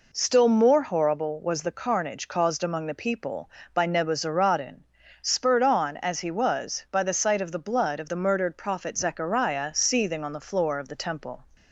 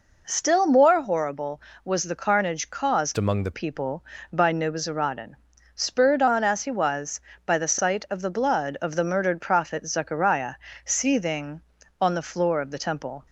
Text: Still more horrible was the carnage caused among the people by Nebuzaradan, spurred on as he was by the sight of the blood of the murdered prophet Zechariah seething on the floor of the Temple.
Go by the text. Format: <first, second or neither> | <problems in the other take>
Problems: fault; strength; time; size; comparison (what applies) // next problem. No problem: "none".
first | changes voice from "among" to "the"; from 3.1 to 3.5 s; 0.4 s long // pauses between "Zechariah" and "seething"; slight; at 10.5 s; 0.32 s long